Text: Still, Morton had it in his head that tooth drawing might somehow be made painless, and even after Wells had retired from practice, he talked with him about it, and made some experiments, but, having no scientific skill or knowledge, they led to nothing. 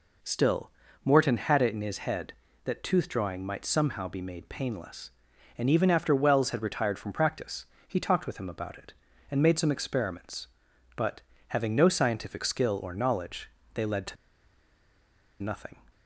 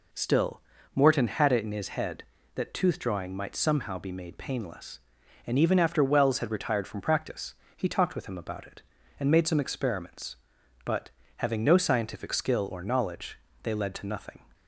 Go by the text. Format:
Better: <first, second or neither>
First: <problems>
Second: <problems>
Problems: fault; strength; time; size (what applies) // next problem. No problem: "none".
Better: second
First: pauses between "to" and "nothing"; strong; at 14.1 s; 1.2 s long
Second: none